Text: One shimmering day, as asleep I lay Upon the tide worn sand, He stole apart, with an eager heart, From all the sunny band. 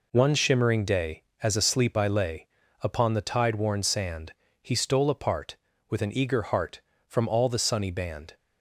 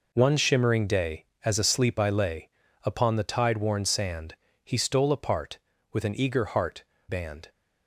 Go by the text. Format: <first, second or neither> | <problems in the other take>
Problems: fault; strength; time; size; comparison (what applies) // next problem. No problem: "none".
first | pauses between "lay" and "Upon"; slight; at 2.4 s; 0.34 s long; slight in the first // skips "From all the sunny"; at 6.9 s